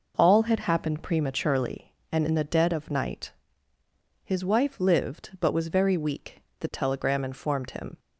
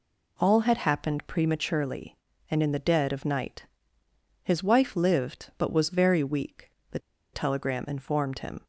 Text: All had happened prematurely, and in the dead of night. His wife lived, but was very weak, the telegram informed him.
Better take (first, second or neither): first